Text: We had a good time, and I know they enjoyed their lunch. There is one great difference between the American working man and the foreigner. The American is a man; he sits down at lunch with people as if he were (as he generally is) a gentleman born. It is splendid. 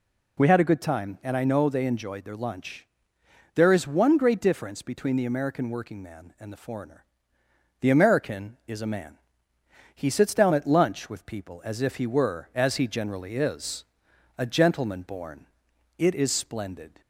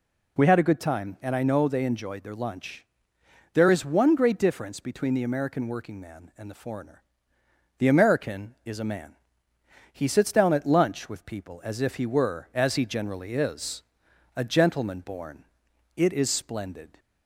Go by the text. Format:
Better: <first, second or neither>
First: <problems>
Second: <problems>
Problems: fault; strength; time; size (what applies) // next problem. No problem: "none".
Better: neither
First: none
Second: none